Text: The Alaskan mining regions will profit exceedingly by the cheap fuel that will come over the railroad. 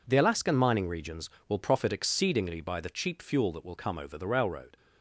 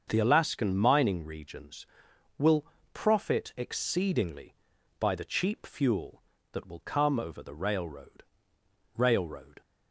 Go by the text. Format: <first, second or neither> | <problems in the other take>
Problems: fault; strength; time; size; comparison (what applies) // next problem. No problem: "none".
first | starts louder than the rest; until 1.0 s; 6.5 dB // pauses between "will" and "profit"; slight; at 2.6 s; 0.30 s long // says "railroad" twice; at 8.9 s